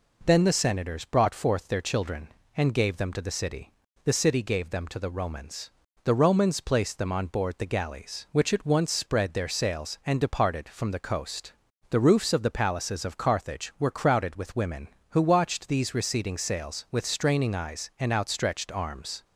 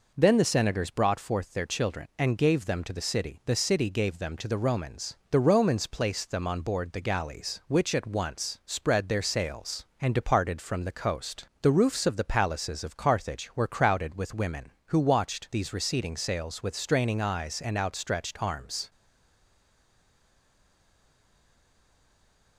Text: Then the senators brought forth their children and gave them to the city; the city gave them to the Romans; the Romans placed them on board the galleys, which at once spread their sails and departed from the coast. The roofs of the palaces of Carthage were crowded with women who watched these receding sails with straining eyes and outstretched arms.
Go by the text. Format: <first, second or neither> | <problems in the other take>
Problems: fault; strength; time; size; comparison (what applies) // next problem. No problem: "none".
first | stays silent after the last word; strong; from 18.9 s on; 3.6 s long